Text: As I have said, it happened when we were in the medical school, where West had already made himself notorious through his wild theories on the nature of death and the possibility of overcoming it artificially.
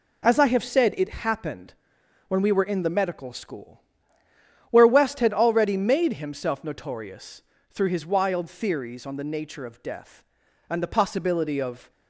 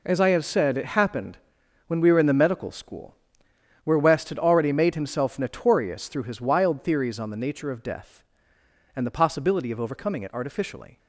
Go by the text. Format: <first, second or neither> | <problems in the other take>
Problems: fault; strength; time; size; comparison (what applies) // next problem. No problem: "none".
second | pauses between "happened" and "when"; noticeable; at 1.7 s; 0.56 s long; noticeable in the second // pauses between "notorious" and "through"; slight; at 7.4 s; 0.28 s long // stops before "overcoming it artificially"; at 11.8 s